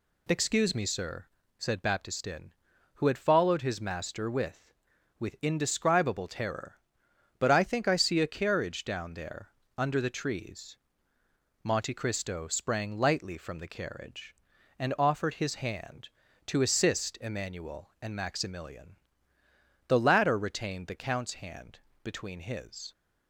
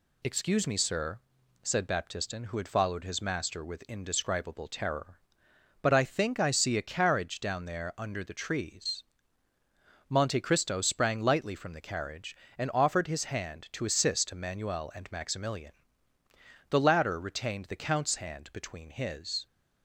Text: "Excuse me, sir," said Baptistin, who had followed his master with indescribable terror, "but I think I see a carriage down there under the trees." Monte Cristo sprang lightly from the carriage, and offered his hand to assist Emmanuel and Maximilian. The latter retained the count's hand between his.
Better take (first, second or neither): second